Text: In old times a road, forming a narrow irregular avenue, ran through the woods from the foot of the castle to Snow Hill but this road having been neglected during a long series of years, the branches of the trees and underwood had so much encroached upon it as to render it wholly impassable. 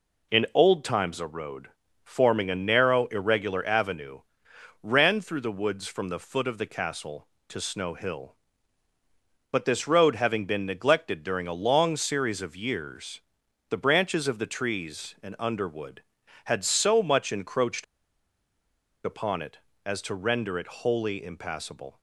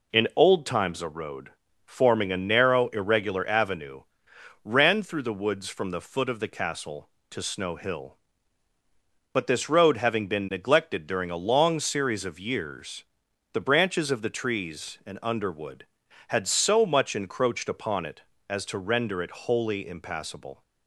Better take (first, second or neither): second